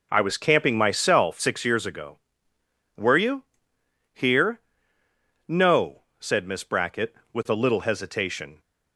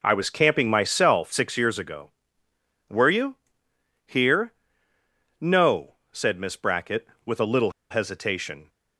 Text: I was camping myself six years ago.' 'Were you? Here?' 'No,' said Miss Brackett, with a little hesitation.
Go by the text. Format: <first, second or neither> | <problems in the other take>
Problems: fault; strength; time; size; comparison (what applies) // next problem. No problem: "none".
first | pauses between "little" and "hesitation"; slight; at 7.7 s; 0.20 s long